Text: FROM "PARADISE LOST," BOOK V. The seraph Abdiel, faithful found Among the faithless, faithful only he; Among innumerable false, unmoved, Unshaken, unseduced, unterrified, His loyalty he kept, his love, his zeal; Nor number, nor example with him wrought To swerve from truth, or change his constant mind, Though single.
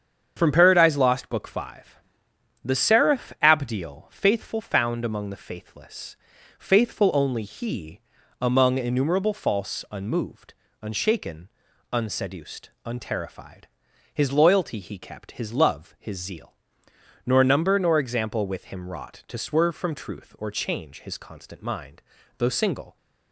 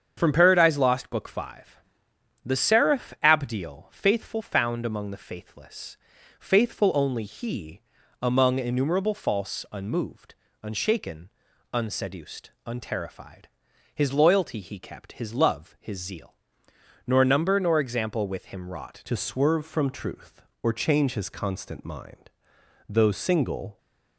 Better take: first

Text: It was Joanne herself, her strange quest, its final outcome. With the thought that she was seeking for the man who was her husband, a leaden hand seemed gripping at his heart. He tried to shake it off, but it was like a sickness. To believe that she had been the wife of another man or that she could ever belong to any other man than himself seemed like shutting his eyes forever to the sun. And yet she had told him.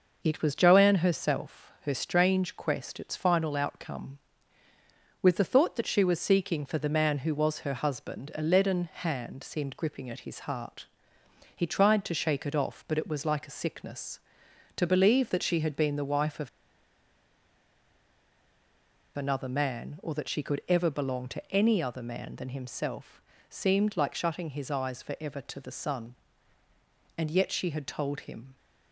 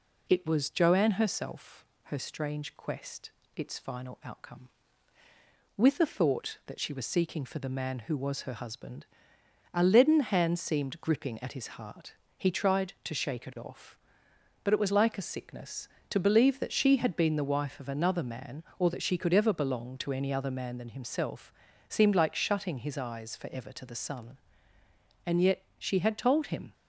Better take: second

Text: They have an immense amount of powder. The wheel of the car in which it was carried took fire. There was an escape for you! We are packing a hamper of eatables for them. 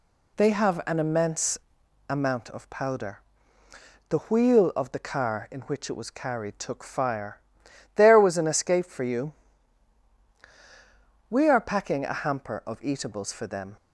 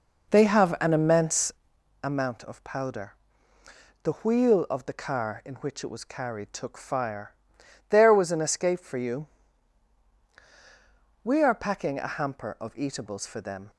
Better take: first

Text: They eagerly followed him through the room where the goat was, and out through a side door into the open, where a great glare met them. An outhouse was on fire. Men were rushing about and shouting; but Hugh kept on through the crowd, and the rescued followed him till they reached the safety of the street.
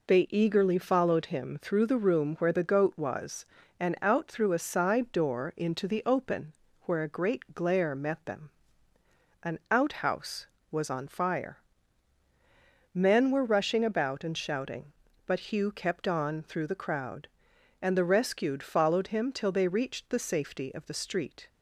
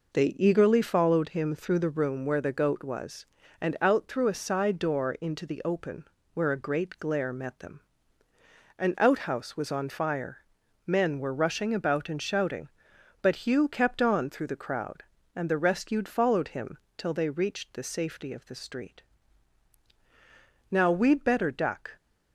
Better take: first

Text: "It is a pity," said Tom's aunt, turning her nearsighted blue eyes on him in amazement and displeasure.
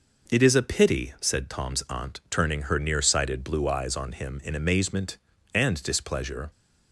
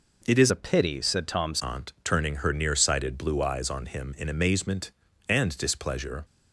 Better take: first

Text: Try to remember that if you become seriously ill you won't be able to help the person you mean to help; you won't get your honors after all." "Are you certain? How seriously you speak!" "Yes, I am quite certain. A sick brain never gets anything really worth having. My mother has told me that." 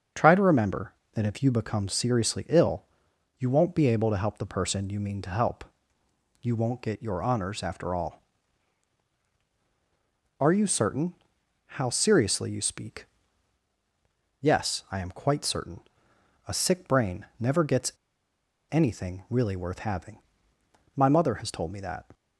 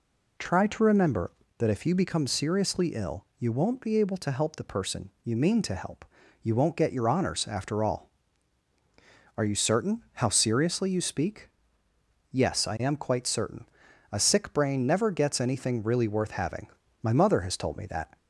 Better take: second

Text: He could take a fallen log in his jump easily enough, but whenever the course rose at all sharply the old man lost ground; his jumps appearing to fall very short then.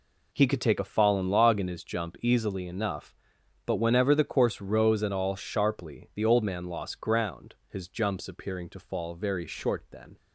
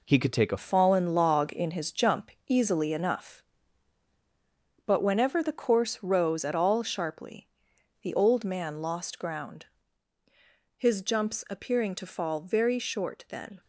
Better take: first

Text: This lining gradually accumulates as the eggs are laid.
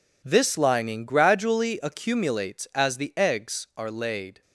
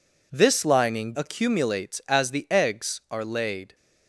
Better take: first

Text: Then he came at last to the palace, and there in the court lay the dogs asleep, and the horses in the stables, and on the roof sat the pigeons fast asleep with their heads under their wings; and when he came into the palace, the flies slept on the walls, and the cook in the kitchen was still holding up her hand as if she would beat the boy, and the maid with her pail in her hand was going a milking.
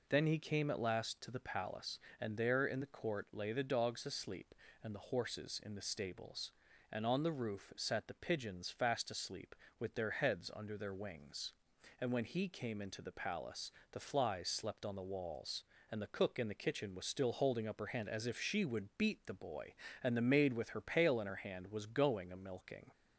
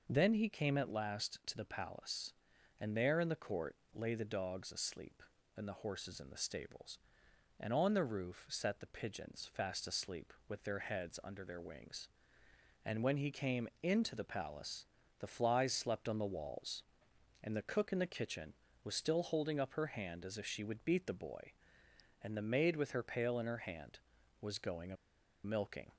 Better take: first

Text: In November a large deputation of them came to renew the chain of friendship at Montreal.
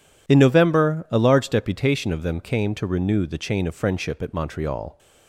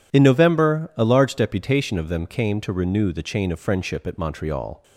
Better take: neither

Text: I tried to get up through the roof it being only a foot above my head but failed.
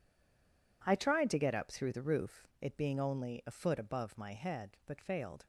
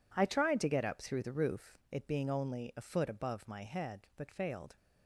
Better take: second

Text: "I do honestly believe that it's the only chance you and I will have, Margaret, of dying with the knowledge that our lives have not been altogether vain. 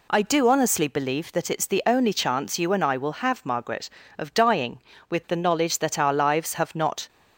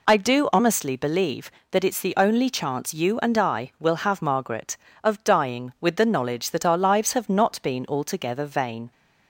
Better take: second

